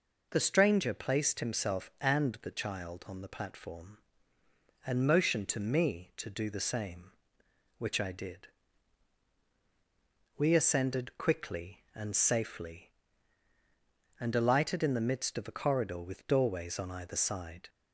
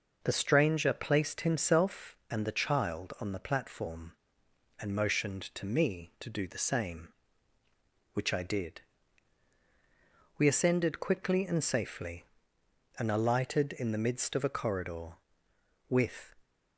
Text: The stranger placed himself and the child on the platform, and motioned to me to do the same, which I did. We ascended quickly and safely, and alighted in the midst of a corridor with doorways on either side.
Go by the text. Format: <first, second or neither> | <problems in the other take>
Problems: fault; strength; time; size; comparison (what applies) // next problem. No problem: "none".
first | stops before "doorways on either side"; at 16.4 s